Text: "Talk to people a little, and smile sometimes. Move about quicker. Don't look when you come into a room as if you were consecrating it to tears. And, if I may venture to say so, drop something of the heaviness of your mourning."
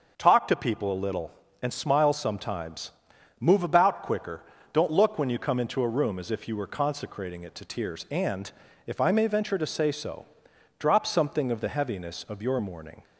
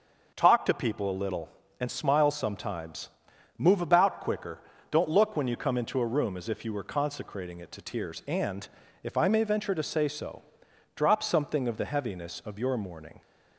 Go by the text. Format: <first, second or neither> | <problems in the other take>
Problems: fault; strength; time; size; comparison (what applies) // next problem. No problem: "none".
neither | starts louder than the rest; noticeable; the same in both